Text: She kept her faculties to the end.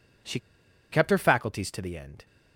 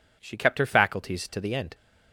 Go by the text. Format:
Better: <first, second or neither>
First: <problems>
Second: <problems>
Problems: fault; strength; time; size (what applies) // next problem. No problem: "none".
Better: second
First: pauses between "She" and "kept"; noticeable; at 0.3 s; 0.52 s long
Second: none